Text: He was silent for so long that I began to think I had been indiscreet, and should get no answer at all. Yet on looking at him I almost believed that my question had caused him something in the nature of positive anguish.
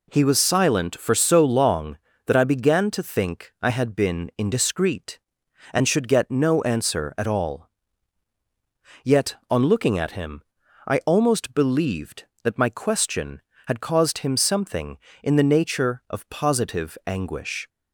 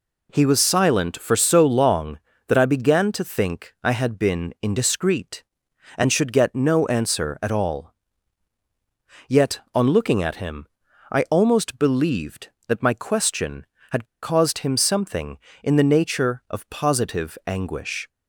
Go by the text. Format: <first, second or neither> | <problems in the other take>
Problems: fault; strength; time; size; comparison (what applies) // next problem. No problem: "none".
first | pauses between "him" and "I"; at 10.6 s; 0.44 s long; also in the first // pauses between "had" and "caused"; slight; at 14.0 s; 0.17 s long